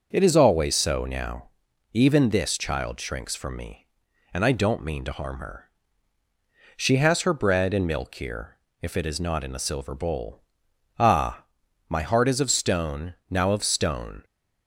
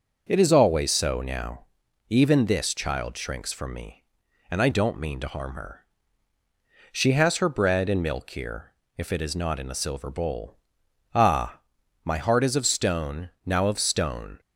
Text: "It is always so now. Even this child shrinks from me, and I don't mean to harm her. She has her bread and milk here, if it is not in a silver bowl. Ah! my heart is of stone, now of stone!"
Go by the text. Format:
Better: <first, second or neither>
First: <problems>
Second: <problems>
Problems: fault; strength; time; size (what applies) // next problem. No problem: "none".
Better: neither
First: starts louder than the rest; until 1.1 s; 6 dB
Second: starts louder than the rest; until 1.2 s; 6 dB